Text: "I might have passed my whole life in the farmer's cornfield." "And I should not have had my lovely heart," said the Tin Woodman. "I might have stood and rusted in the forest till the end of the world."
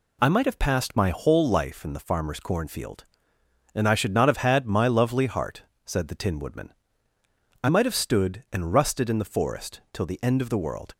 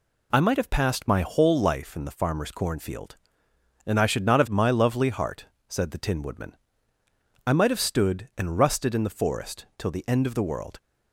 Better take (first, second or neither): first